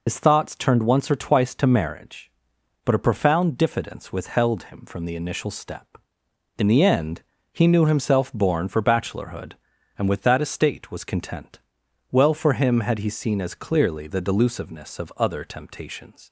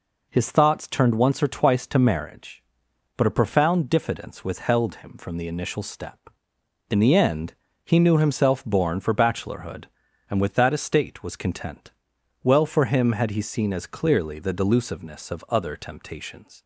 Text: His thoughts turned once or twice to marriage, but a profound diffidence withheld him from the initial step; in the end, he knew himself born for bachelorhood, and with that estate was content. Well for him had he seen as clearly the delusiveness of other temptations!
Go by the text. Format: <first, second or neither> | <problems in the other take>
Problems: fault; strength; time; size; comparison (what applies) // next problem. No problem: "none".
second | loses the start of "His"; at 0.0 s; 90 ms